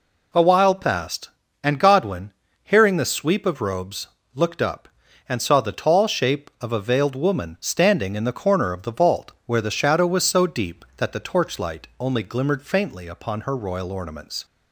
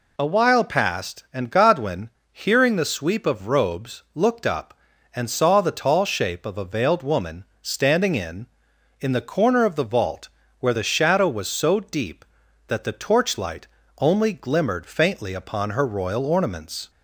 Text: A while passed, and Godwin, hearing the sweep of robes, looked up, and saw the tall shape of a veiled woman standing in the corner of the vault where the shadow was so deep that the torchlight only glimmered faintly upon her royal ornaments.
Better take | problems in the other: first | pauses between "woman" and "standing"; slight; at 7.4 s; 0.16 s long // says "in" twice; at 8.9 s // pauses between "vault" and "where"; slight; at 10.2 s; 0.32 s long; slight in the first // pauses between "torchlight" and "only"; slight; at 13.6 s; 0.34 s long

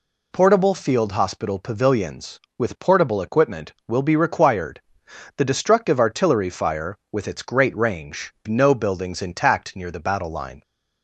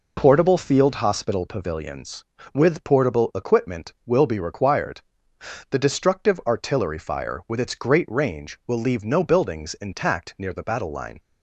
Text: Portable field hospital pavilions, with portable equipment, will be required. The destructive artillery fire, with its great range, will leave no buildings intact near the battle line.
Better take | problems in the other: second | skips "will leave"; at 8.3 s

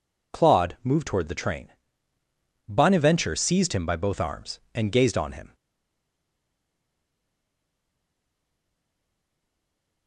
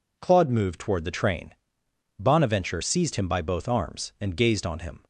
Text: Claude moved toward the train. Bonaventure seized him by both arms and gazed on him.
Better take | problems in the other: second | stays silent after the last word; strong; from 5.5 s on; 4.5 s long

